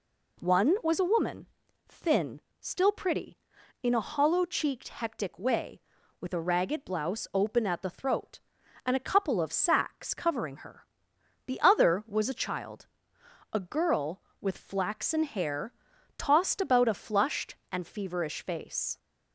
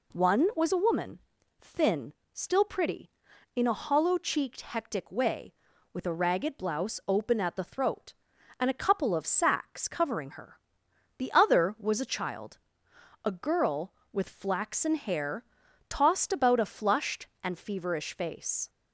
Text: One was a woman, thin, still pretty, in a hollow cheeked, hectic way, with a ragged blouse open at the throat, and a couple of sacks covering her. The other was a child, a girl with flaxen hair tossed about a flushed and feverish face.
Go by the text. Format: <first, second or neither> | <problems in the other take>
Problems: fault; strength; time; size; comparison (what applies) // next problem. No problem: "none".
neither | pauses between "hair" and "tossed"; noticeable; the same in both